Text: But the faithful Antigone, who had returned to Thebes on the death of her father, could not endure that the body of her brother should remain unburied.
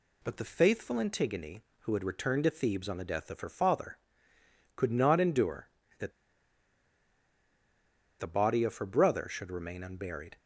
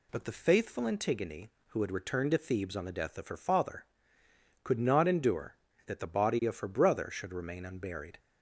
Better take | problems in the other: second | pauses between "that" and "the"; strong; at 6.1 s; 2.0 s long

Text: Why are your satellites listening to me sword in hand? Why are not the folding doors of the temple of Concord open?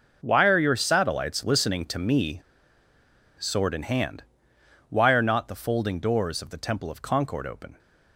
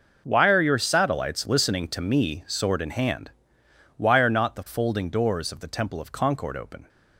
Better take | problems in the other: second | pauses between "me" and "sword"; noticeable; at 2.4 s; 0.96 s long

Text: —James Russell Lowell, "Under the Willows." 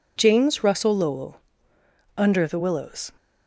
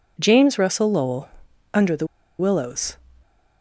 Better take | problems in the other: first | pauses between "the" and "Willows"; slight; at 2.0 s; 0.32 s long

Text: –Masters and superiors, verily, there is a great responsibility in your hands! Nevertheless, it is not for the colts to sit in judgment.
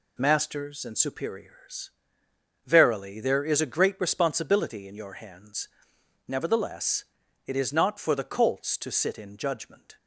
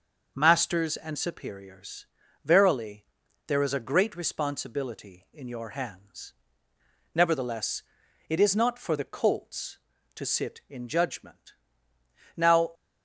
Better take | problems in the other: first | goes on to say "Now"; slight; from 12.3 s on; 0.34 s long

